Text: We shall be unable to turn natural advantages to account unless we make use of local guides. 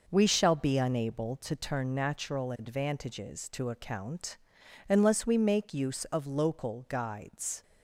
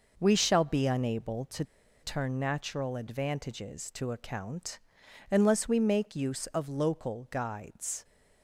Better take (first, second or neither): first